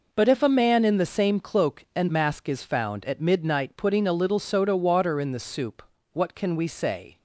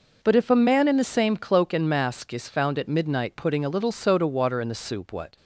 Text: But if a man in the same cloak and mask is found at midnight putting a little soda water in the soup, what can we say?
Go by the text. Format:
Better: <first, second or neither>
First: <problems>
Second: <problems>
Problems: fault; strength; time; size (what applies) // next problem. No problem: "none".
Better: first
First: none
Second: stops before "can we say"; at 5.3 s